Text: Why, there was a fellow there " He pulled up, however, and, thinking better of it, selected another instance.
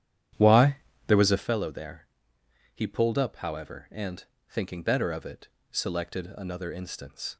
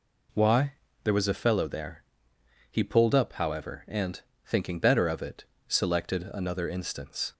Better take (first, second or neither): second